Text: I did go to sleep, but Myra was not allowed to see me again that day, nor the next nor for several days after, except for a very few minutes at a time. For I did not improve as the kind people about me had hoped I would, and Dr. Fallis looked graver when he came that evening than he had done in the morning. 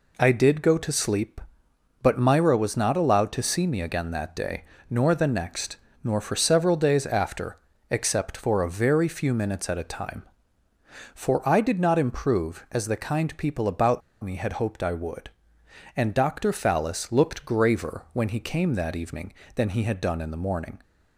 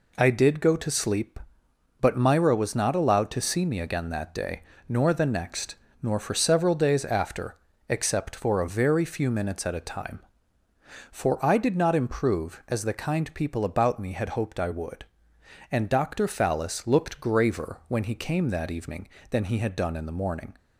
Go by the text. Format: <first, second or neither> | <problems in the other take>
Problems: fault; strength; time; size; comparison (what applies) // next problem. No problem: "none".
second | pauses between "next" and "nor"; slight; at 5.7 s; 0.30 s long; slight in the second // pauses between "about" and "me"; slight; at 14.0 s; 0.22 s long